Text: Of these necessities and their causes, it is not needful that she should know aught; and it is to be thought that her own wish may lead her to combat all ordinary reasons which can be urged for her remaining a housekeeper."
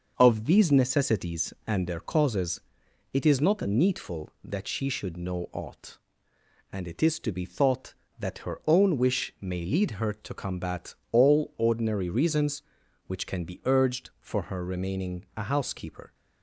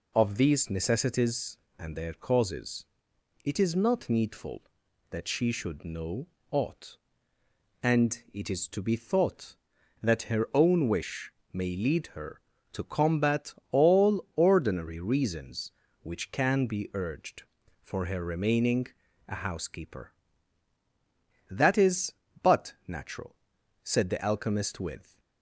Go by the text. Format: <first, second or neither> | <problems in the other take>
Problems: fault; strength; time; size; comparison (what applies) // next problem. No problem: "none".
first | pauses between "know" and "aught"; slight; at 6.2 s; 0.24 s long // pauses between "wish" and "may"; slight; at 11.3 s; 0.22 s long // pauses between "combat" and "all"; slight; at 13.5 s; 0.18 s long; slight in the first // pauses between "remaining" and "a"; at 18.8 s; 0.40 s long // goes on to say "That is but natural said the alchemist with"; strong; from 21.5 s on; 3.6 s long